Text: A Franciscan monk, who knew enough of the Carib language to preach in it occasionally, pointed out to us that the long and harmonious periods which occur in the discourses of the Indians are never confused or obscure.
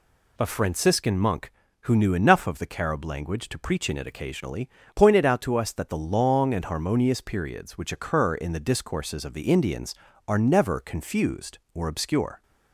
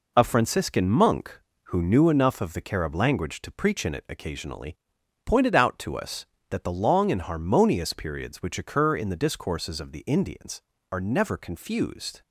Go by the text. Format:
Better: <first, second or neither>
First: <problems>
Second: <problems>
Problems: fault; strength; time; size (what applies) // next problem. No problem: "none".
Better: first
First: none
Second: stops before "or obscure"; at 12.2 s